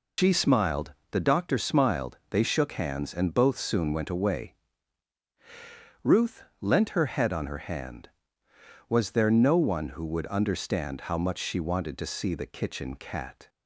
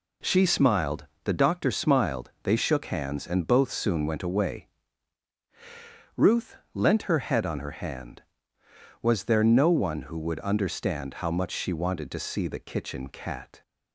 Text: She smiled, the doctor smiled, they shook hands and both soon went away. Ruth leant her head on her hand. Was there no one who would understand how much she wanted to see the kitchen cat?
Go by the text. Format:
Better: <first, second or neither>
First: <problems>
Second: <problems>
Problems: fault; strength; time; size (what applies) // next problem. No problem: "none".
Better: second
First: loses the start of "She"; at 0.1 s; 95 ms // pauses between "Ruth" and "leant"; slight; at 6.4 s; 0.18 s long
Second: pauses between "Ruth" and "leant"; slight; at 6.5 s; 0.18 s long